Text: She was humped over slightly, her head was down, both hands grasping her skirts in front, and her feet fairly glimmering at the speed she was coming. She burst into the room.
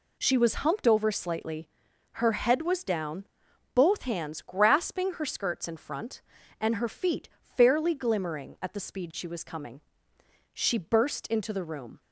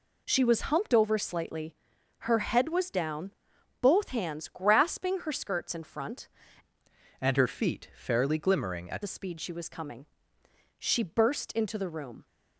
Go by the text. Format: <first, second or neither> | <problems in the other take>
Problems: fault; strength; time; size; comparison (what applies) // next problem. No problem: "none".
first | changes voice from "and" to "at"; from 7.2 to 9.0 s; 1.8 s long